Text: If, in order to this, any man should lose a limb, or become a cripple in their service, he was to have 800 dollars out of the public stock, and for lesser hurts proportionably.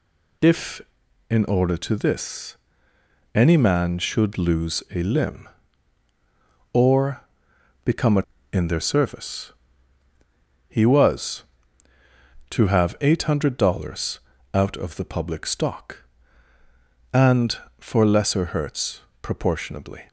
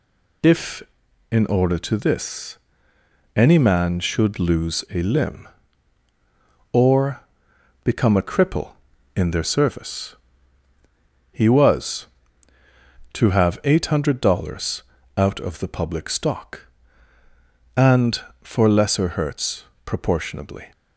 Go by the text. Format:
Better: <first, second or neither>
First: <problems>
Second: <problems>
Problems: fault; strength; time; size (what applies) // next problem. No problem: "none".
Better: second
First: pauses between "or" and "become"; noticeable; at 7.2 s; 0.64 s long // skips "cripple"; at 8.3 s // pauses between "dollars" and "out"; slight; at 14.1 s; 0.34 s long // pauses between "hurts" and "proportionably"; slight; at 19.0 s; 0.22 s long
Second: pauses between "or" and "become"; noticeable; at 7.2 s; 0.64 s long // pauses between "dollars" and "out"; slight; at 14.8 s; 0.34 s long // pauses between "hurts" and "proportionably"; slight; at 19.6 s; 0.22 s long